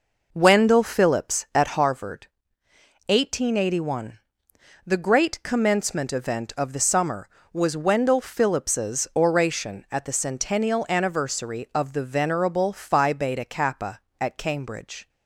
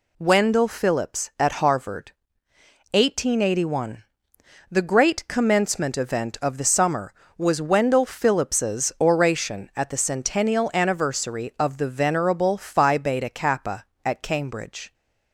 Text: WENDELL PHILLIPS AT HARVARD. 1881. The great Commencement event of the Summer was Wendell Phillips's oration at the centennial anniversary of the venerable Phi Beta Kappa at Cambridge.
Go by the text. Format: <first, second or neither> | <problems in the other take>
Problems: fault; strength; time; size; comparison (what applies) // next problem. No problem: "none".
second | starts louder than the rest; noticeable; until 1.7 s; 5 dB